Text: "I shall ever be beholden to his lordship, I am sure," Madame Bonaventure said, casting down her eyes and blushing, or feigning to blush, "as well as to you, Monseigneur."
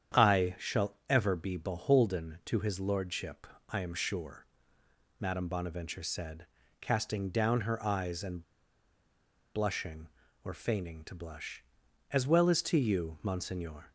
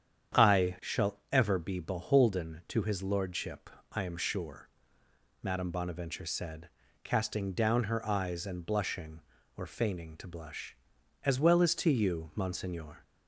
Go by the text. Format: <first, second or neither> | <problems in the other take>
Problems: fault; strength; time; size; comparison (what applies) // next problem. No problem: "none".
second | starts louder than the rest; strong; until 1.3 s; 9 dB; strong in the second // pauses between "and" and "blushing"; at 8.4 s; 1.1 s long